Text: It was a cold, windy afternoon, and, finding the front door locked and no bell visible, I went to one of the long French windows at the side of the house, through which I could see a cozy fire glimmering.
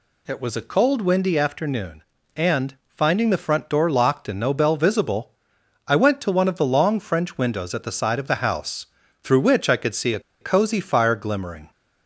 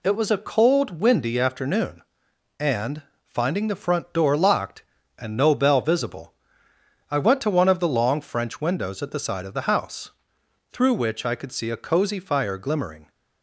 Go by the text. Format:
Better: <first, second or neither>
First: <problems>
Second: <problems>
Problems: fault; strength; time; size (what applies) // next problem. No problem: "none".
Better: second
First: pauses between "a" and "cozy"; slight; at 10.1 s; 0.21 s long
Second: none